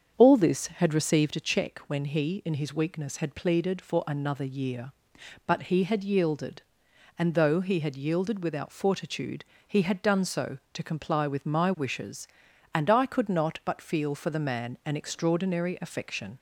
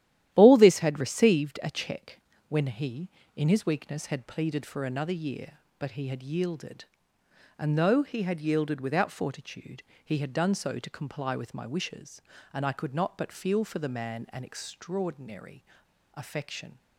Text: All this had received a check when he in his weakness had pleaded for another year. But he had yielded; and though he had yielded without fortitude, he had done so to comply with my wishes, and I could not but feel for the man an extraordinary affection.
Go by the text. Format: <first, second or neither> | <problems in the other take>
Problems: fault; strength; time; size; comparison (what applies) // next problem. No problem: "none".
first | starts louder than the rest; strong; until 1.3 s; 12.5 dB; strong in the first // pauses between "check" and "when"; slight; at 2.1 s; 0.30 s long // pauses between "extraordinary" and "affection"; noticeable; at 15.6 s; 0.50 s long